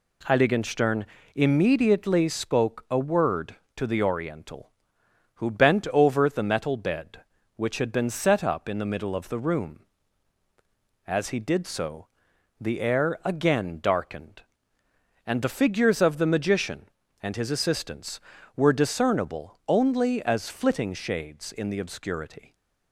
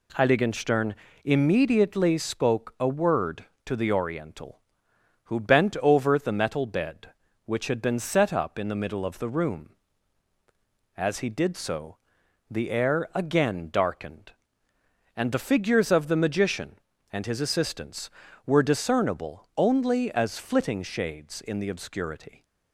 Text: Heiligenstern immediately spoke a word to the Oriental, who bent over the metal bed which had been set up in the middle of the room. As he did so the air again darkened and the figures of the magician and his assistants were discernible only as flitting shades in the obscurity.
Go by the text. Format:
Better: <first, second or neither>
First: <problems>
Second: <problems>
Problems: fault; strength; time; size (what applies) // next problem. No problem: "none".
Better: neither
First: pauses between "Heiligenstern" and "immediately"; slight; at 1.0 s; 0.28 s long // pauses between "so" and "the"; noticeable; at 12.0 s; 0.52 s long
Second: pauses between "Heiligenstern" and "immediately"; slight; at 0.9 s; 0.28 s long // pauses between "so" and "the"; noticeable; at 11.9 s; 0.52 s long